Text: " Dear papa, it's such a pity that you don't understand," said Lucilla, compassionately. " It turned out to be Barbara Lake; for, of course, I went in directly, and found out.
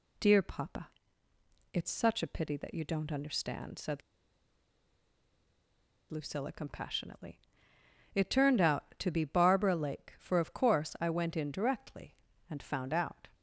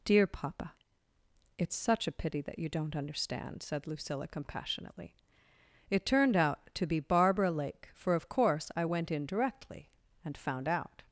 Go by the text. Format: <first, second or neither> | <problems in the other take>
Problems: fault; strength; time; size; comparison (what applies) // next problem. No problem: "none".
second | pauses between "said" and "Lucilla"; strong; at 4.0 s; 2.0 s long